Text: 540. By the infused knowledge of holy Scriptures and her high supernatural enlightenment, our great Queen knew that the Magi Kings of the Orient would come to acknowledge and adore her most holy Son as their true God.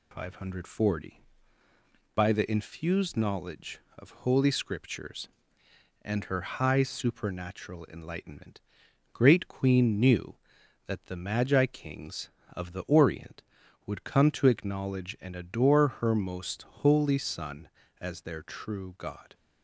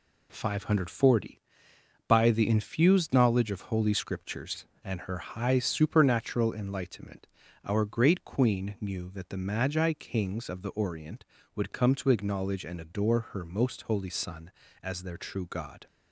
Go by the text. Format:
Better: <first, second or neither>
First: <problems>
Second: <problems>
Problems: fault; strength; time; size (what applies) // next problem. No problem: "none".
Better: second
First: skips "our"; at 8.8 s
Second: none